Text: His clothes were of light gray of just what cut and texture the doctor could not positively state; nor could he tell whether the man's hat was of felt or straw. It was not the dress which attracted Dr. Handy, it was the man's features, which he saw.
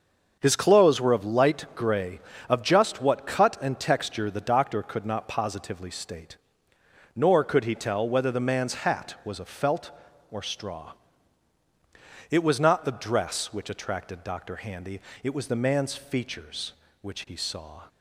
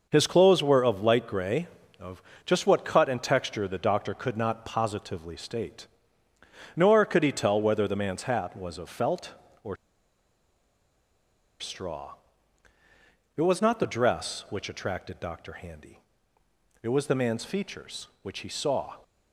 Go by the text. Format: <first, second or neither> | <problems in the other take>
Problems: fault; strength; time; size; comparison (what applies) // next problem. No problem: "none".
first | starts louder than the rest; noticeable; until 1.1 s; 6 dB; also in the first // pauses between "of" and "just"; slight; at 2.2 s; 0.24 s long // pauses between "or" and "straw"; strong; at 9.7 s; 1.8 s long